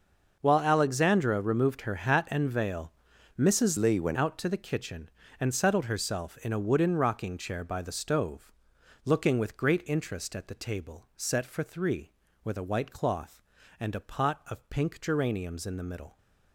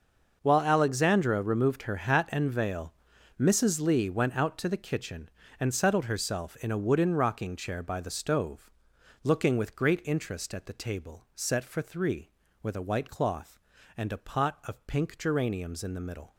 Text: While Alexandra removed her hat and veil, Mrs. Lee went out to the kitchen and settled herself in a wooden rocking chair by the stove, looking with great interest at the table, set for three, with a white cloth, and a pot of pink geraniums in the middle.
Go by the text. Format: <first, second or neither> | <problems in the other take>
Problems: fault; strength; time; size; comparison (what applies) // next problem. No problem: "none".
second | starts louder than the rest; until 1.4 s; 6 dB; also in the second // changes voice from "Lee" to "went"; from 3.7 to 4.1 s; 0.4 s long